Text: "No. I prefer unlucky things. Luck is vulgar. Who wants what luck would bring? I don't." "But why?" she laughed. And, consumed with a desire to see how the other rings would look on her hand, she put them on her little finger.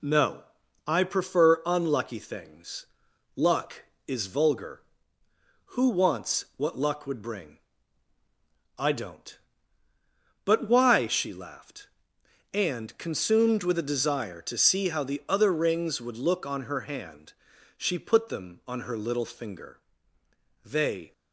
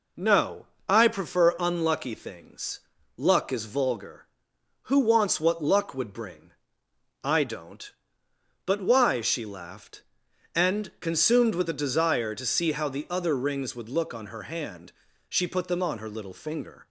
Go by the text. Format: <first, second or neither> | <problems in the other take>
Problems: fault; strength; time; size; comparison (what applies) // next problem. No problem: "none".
second | goes on to say "They"; slight; from 20.6 s on; 0.48 s long